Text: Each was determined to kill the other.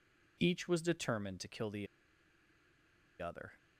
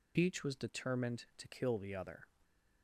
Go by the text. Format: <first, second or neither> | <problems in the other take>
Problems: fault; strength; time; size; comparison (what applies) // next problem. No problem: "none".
second | pauses between "the" and "other"; strong; at 1.8 s; 1.3 s long